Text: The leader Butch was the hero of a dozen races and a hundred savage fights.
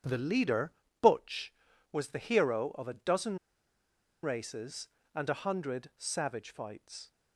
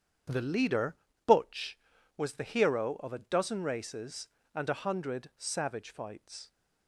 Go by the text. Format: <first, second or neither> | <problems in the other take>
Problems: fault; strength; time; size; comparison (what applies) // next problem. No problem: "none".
second | starts louder than the rest; strong; until 1.3 s; 8.5 dB; strong in the second // pauses between "leader" and "Butch"; slight; at 0.7 s; 0.30 s long; slight in the second // pauses between "dozen" and "races"; noticeable; at 3.3 s; 0.85 s long